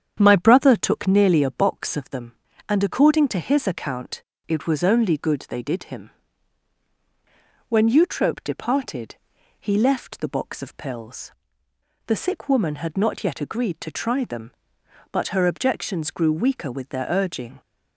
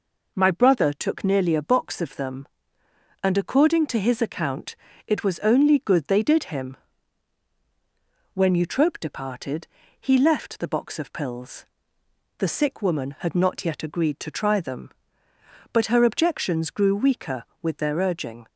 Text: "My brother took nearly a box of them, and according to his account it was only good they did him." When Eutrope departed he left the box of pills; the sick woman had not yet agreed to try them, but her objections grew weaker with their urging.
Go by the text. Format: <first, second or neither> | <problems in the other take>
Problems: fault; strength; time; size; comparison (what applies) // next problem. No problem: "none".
second | starts louder than the rest; strong; until 1.3 s; 8.5 dB // pauses between "account" and "it"; slight; at 4.2 s; 0.26 s long; slight in the second // pauses between "departed" and "he"; noticeable; at 9.1 s; 0.46 s long; slight in the second